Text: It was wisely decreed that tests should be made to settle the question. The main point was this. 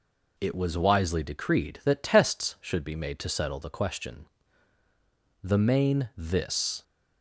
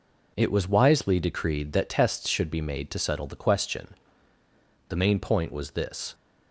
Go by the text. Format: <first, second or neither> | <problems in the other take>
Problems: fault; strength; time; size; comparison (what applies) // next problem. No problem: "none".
second | skips "point was"; at 6.1 s